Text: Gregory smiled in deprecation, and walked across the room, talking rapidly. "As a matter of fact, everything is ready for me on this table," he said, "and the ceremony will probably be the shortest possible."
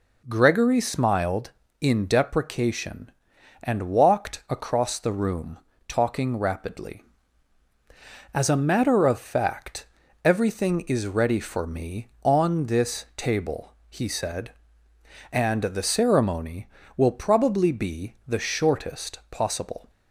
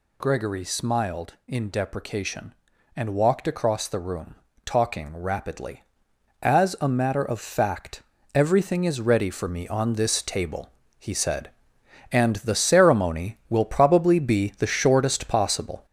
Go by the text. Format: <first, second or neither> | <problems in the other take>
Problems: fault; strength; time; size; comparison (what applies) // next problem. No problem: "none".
first | gets louder; noticeable; throughout; 5 dB